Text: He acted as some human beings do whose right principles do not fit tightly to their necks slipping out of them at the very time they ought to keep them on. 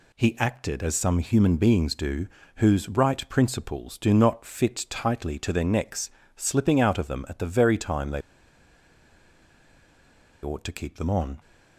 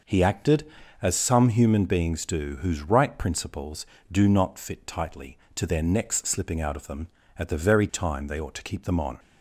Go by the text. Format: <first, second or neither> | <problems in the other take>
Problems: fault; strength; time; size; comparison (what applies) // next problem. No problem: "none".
second | pauses between "do" and "whose"; slight; at 2.2 s; 0.30 s long // pauses between "necks" and "slipping"; slight; at 6.1 s; 0.26 s long // pauses between "they" and "ought"; strong; at 8.2 s; 2.2 s long